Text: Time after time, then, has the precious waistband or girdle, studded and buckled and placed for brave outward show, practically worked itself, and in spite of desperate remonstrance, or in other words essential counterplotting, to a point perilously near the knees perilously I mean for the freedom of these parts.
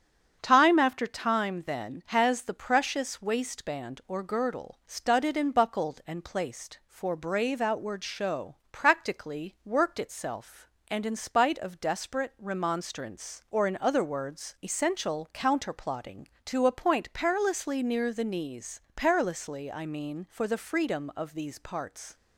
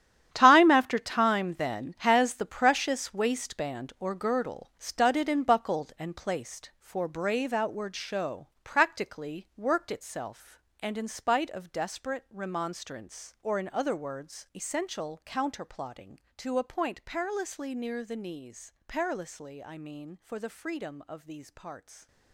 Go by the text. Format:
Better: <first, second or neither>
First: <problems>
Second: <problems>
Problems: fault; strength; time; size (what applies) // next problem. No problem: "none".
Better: first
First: starts louder than the rest; strong; until 1.4 s; 7.5 dB // pauses between "knees" and "perilously"; slight; at 18.7 s; 0.16 s long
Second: gets quieter; strong; throughout; 13 dB // starts louder than the rest; strong; until 1.3 s; 10 dB // pauses between "knees" and "perilously"; slight; at 18.7 s; 0.16 s long